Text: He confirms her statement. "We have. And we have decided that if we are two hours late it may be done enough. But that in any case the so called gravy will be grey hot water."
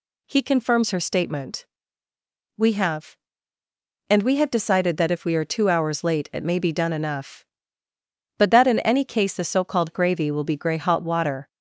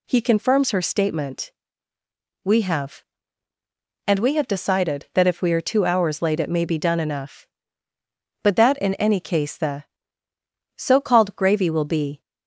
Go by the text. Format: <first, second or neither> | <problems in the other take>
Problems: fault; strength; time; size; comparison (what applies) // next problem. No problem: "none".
first | stops before "grey hot water"; at 12.2 s